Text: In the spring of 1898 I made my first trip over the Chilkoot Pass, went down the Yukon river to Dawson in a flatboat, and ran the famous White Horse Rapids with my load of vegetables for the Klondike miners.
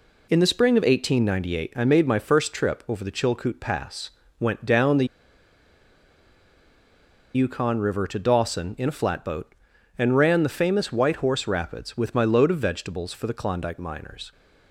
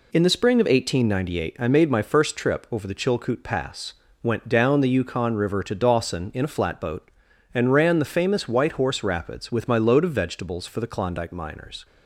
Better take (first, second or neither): second